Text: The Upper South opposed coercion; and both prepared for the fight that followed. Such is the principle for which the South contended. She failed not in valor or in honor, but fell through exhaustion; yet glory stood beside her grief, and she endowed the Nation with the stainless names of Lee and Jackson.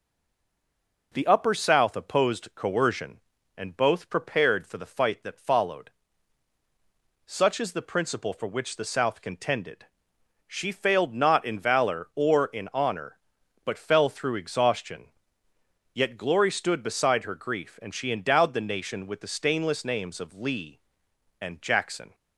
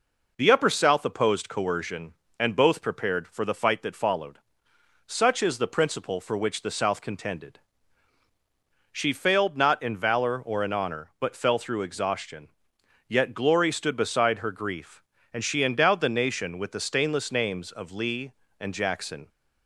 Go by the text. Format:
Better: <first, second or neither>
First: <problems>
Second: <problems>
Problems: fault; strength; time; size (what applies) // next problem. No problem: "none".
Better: second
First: stays silent before the first word; until 1.1 s; 1.1 s long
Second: none